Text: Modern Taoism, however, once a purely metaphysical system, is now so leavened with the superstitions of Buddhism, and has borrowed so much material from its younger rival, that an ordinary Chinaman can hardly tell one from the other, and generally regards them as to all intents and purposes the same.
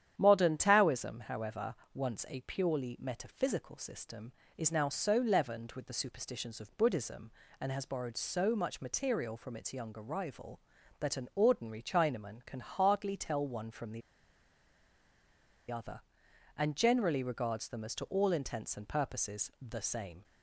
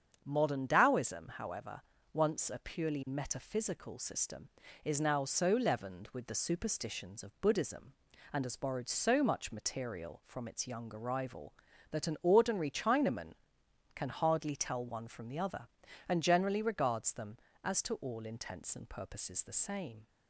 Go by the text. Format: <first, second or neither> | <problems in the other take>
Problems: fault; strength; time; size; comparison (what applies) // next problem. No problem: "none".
second | starts louder than the rest; strong; until 1.1 s; 9.5 dB; strong in the second // pauses between "the" and "other"; strong; at 14.0 s; 1.7 s long